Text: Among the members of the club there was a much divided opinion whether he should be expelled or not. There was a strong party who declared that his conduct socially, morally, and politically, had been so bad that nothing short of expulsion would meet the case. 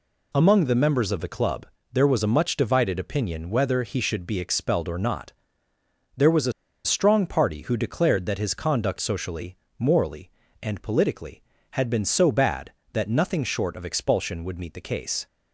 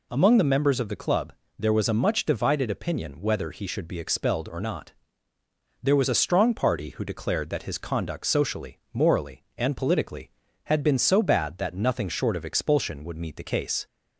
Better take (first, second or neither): second